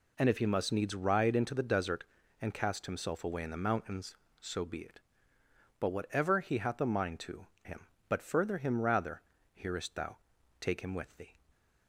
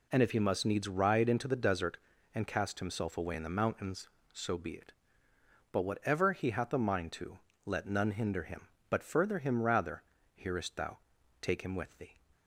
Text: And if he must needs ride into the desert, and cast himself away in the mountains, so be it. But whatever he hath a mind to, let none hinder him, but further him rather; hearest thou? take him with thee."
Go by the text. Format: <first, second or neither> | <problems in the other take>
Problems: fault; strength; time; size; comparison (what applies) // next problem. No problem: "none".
second | skips "let none hinder"; at 7.5 s